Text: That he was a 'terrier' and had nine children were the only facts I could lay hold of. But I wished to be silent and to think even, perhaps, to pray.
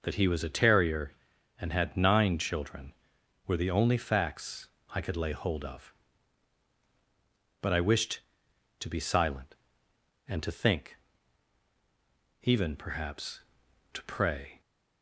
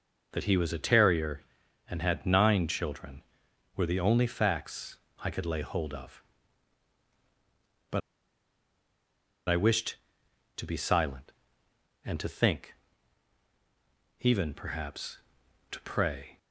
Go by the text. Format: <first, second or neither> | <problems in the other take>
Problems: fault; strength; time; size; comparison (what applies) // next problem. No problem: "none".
first | pauses between "facts" and "I"; slight; at 4.9 s; 0.22 s long; slight in the first // pauses between "But" and "I"; strong; at 8.0 s; 1.4 s long // pauses between "think" and "even"; strong; at 12.7 s; 1.4 s long; strong in the first